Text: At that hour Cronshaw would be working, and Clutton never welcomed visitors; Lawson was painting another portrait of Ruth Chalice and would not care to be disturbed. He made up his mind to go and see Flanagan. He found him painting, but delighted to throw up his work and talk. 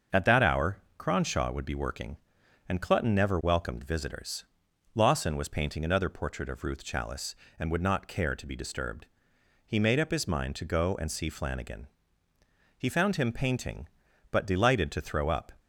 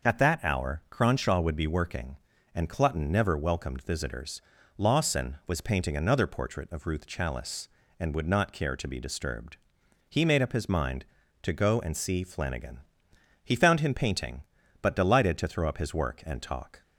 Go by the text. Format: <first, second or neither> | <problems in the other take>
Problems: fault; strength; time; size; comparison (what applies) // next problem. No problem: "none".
second | starts louder than the rest; until 1.3 s; 6.5 dB; noticeable in the second // pauses between "hour" and "Cronshaw"; slight; at 0.7 s; 0.20 s long // stops before "his work and talk"; at 15.5 s